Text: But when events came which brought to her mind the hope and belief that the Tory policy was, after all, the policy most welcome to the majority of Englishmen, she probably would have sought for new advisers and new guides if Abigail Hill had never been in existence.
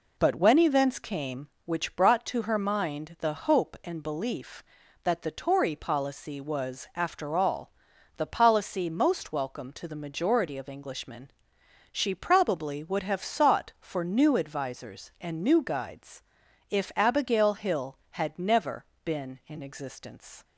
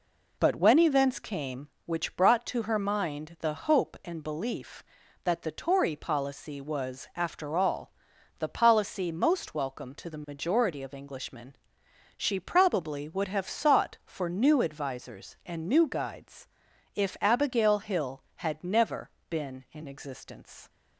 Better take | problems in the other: neither | pauses between "guides" and "if"; noticeable; the same in both // pauses between "never" and "been"; slight; the same in both

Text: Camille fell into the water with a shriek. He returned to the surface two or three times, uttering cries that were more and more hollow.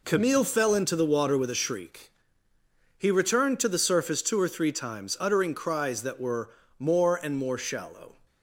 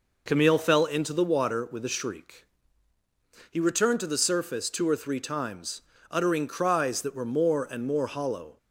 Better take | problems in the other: second | pauses between "were" and "more"; slight; at 6.5 s; 0.28 s long // says "shallow" for "hollow"; at 7.5 s

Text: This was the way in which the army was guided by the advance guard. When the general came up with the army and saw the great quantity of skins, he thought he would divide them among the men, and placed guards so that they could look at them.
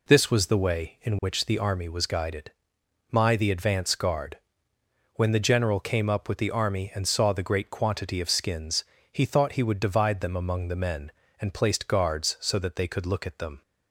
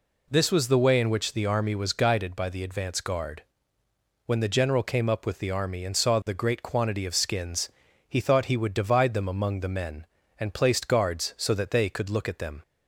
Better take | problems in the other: second | says "my" for "by"; at 3.1 s

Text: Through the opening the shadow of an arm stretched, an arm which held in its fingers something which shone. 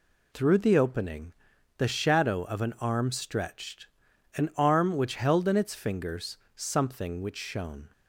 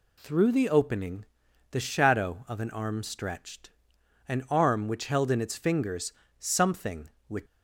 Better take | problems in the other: first | pauses between "opening" and "the"; at 1.2 s; 0.44 s long; also in the first // pauses between "fingers" and "something"; slight; at 6.1 s; 0.26 s long; slight in the first // stops before "shone"; at 7.4 s

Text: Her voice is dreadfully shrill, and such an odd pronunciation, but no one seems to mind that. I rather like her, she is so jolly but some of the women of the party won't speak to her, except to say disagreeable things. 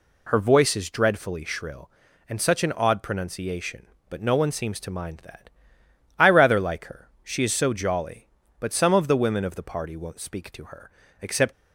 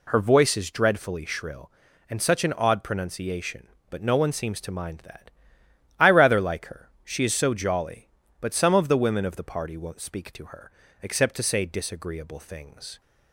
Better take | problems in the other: second | stops before "to say disagreeable things"; at 11.5 s

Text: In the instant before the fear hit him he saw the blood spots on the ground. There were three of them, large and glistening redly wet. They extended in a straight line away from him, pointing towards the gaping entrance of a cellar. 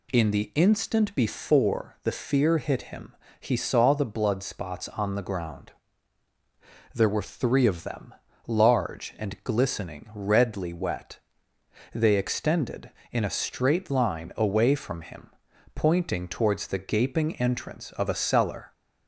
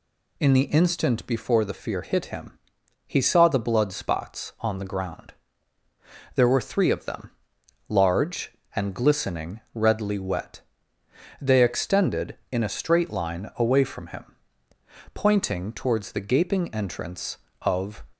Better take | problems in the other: first | pauses between "him" and "he"; noticeable; at 2.5 s; 0.48 s long; slight in the first // stops before "a cellar"; at 18.1 s

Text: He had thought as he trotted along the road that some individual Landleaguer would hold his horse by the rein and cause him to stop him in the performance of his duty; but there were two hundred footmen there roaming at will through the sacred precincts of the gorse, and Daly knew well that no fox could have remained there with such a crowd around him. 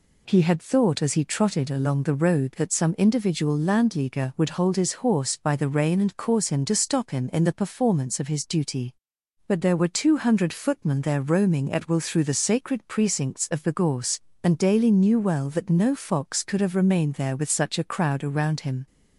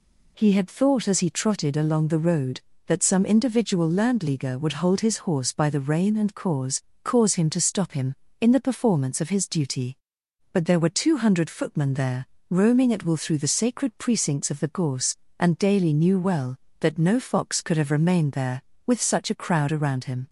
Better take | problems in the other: first | says "cause" twice; at 7.0 s // pauses between "there" and "roaming"; slight; at 12.2 s; 0.24 s long

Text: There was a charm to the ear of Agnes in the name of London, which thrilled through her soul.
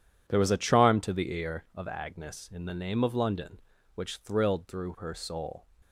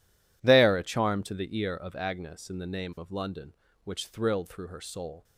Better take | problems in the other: first | skips "was"; at 0.7 s

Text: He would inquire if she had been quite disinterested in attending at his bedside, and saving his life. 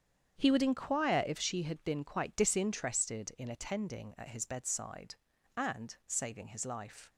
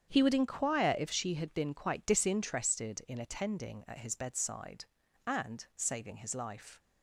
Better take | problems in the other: neither | starts louder than the rest; strong; the same in both

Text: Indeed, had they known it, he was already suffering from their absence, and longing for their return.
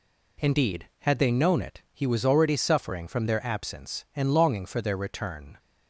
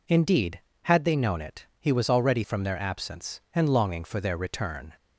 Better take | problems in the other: first | skips "suffering"; at 2.4 s

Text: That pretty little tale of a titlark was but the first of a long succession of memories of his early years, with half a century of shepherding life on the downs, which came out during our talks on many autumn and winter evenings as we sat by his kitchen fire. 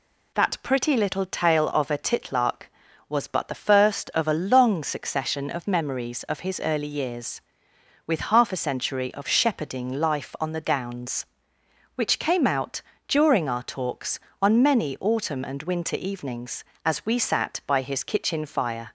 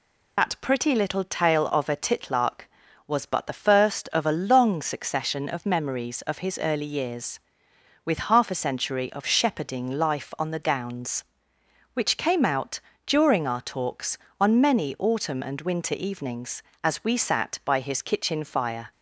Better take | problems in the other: first | loses the start of "That"; at 0.3 s; 50 ms // pauses between "out" and "during"; slight; at 12.7 s; 0.26 s long; slight in the first

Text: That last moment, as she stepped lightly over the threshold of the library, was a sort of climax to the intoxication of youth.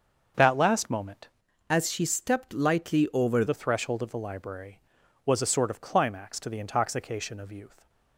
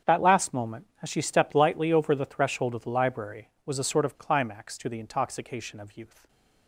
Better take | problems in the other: second | starts louder than the rest; until 1.7 s; 7 dB; strong in the second // changes voice from "as" to "over"; from 1.6 to 3.4 s; 1.8 s long

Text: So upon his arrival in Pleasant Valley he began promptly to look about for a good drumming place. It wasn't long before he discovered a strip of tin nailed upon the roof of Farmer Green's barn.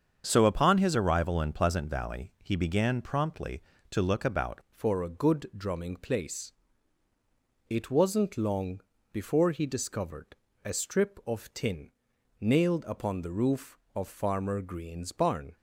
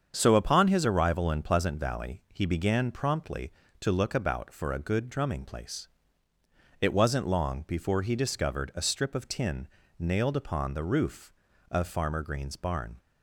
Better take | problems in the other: second | starts louder than the rest; strong; until 1.2 s; 7 dB; strong in the second // changes voice at "for"; from 4.6 s on; 10.9 s long // pauses between "long" and "before"; slight; at 8.8 s; 0.32 s long // pauses between "discovered" and "a"; slight; at 10.3 s; 0.28 s long // pauses between "tin" and "nailed"; noticeable; at 11.8 s; 0.50 s long; slight in the second

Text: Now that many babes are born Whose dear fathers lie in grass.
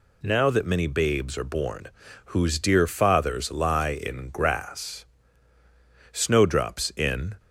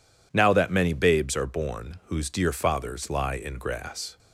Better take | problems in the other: second | pauses between "born" and "Whose"; at 1.8 s; 0.38 s long // goes on to say "Snowdrops in"; noticeable; from 6.1 s on; 1.2 s long

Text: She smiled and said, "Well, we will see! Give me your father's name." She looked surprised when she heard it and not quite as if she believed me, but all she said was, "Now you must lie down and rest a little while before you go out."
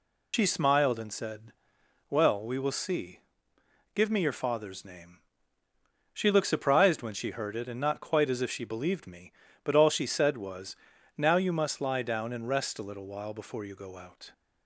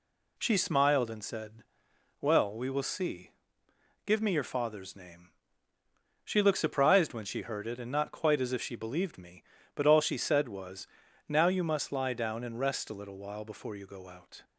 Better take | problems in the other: second | loses the start of "She"; at 0.3 s; 70 ms

